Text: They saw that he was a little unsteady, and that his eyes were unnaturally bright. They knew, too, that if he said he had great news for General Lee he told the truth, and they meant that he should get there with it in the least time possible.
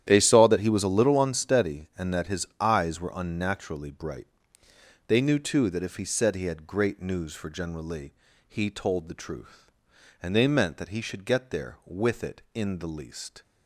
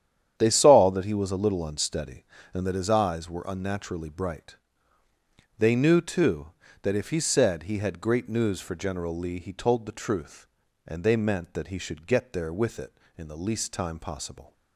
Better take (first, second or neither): second